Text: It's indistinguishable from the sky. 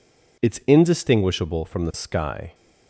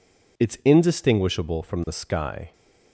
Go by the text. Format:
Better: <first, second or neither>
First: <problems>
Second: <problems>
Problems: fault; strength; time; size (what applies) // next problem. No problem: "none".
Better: neither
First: none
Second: none